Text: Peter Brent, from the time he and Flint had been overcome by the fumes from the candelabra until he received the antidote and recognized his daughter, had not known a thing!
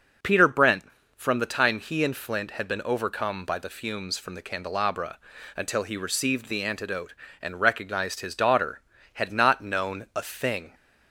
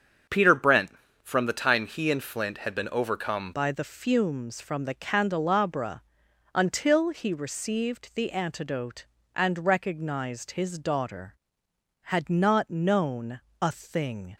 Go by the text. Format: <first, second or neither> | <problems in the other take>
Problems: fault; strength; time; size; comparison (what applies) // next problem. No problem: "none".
first | starts louder than the rest; strong; until 1.6 s; 7.5 dB // changes voice at "by"; from 3.5 s on; 10.8 s long // pauses between "candelabra" and "until"; noticeable; at 6.0 s; 0.52 s long; also in the first // pauses between "known" and "a"; slight; at 13.3 s; 0.20 s long